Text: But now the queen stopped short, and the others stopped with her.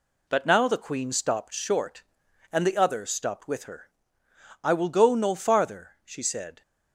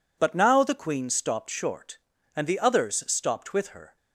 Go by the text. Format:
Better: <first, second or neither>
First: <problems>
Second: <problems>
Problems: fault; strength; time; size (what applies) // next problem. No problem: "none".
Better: second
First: goes on to say "I will go no farther she said"; strong; from 4.6 s on; 1.9 s long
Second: none